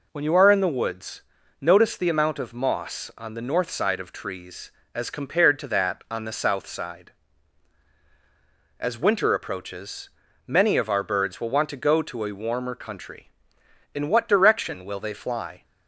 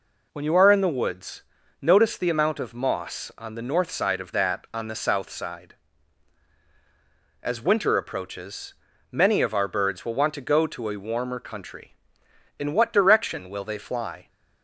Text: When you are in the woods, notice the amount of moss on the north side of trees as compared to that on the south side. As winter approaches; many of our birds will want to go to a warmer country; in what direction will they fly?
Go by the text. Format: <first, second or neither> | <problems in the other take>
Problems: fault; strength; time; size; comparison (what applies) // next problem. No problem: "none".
first | skips "trees as compared to"; at 4.3 s